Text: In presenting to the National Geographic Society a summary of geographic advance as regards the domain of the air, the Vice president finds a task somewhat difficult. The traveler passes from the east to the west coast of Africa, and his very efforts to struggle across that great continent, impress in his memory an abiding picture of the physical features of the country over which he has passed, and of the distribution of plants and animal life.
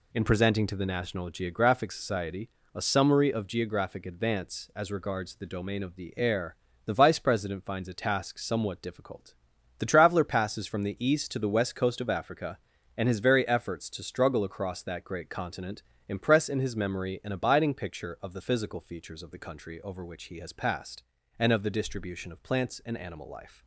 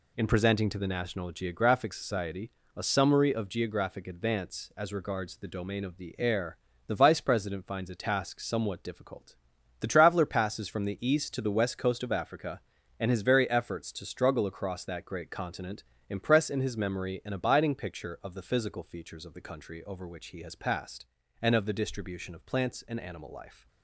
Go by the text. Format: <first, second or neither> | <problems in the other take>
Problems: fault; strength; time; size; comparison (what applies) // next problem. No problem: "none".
neither | pauses between "Society" and "a"; slight; the same in both